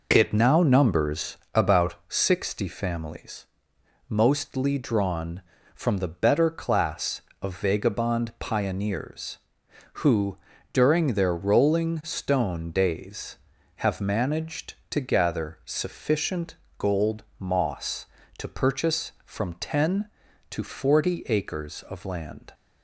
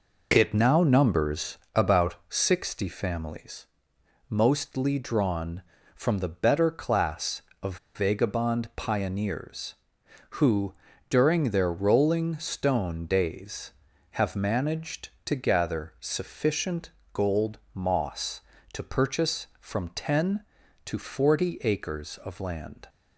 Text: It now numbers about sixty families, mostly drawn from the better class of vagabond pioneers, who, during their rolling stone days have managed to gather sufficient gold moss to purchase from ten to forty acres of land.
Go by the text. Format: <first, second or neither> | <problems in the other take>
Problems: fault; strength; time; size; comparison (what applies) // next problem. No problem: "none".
first | pauses between "numbers" and "about"; slight; at 1.5 s; 0.16 s long; slight in the first // pauses between "about" and "sixty"; slight; at 2.1 s; 0.16 s long; slight in the first // pauses between "of" and "vagabond"; slight; at 7.7 s; 0.18 s long // pauses between "sufficient" and "gold"; slight; at 16.9 s; 0.20 s long; slight in the first // pauses between "gold" and "moss"; slight; at 17.5 s; 0.16 s long; slight in the first